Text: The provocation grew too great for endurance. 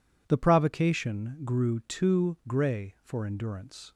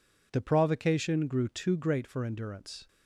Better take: second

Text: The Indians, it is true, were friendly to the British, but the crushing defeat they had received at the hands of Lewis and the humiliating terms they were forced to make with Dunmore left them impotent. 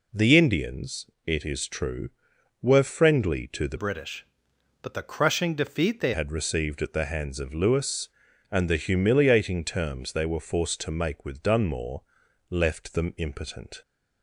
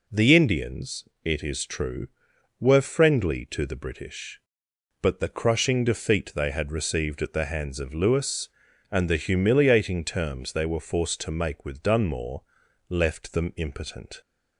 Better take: second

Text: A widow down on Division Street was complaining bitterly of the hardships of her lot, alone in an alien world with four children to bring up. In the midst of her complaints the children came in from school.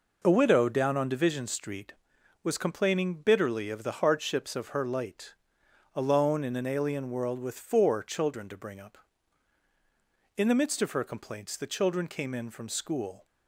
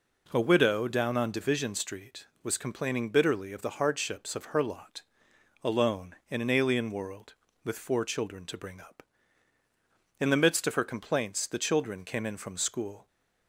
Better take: second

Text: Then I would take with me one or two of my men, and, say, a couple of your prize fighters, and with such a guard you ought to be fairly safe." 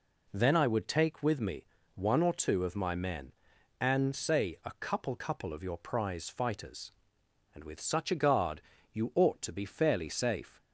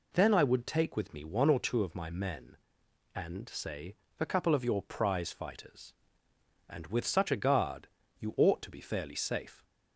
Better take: second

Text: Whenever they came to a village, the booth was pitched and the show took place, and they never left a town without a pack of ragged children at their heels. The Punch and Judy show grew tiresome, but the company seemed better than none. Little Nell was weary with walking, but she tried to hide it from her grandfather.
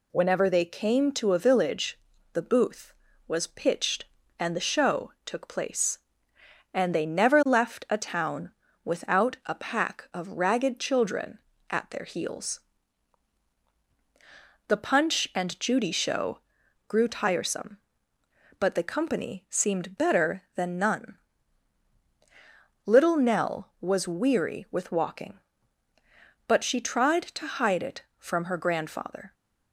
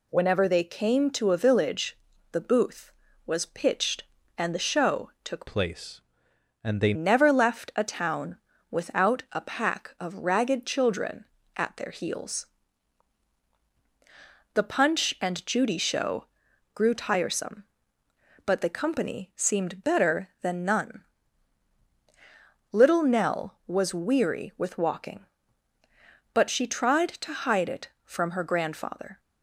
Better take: first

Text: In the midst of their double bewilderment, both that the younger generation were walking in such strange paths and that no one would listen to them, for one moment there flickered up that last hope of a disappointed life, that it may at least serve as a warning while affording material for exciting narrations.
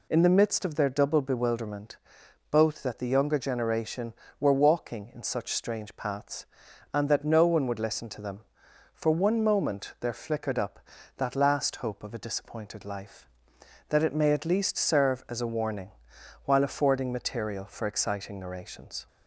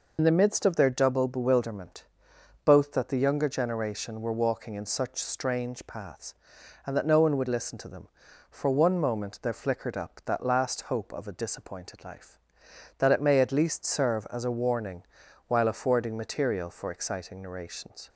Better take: first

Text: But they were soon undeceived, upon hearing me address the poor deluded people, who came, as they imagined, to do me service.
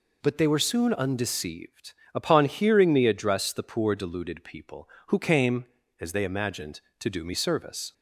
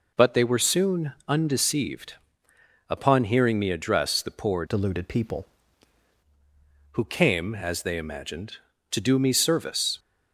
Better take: first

